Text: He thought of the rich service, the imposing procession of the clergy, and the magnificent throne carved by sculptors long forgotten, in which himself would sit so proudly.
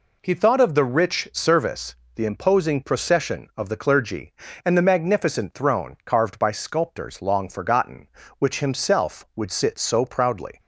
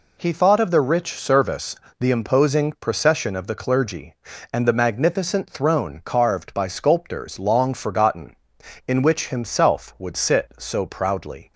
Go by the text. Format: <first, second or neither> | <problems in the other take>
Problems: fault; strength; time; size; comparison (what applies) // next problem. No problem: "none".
second | skips "in"; at 8.2 s